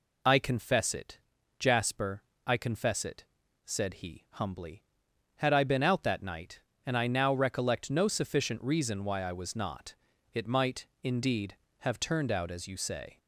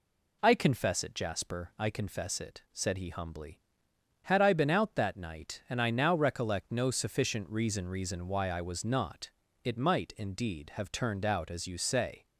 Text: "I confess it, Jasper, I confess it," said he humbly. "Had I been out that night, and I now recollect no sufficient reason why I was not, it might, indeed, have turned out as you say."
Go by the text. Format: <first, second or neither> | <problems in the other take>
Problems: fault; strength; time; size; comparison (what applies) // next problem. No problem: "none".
first | says "reason" twice; at 7.8 s